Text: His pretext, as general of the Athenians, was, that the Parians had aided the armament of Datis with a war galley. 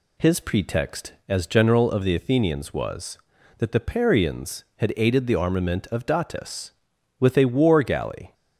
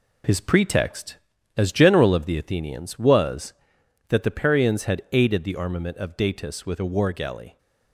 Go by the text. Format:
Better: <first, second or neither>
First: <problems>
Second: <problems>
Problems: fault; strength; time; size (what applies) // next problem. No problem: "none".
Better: first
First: none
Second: gets quieter; noticeable; throughout; 6 dB